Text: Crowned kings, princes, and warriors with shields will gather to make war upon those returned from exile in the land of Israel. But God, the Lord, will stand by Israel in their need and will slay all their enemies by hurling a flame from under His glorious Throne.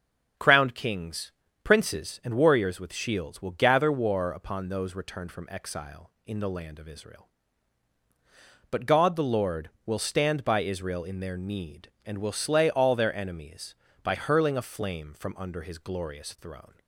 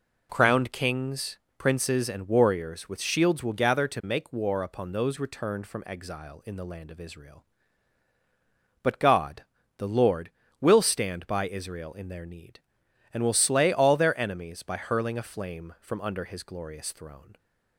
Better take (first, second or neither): second